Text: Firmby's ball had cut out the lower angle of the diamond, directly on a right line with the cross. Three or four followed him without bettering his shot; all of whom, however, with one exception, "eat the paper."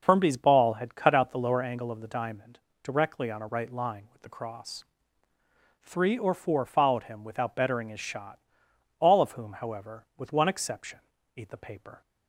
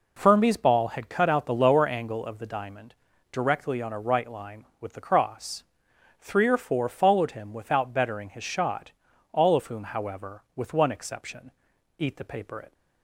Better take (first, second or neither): first